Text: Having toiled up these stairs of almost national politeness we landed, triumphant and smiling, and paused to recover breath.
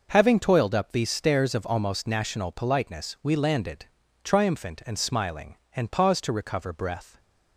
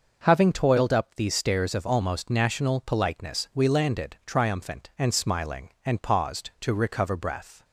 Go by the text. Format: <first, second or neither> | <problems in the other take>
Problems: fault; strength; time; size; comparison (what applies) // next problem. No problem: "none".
neither | none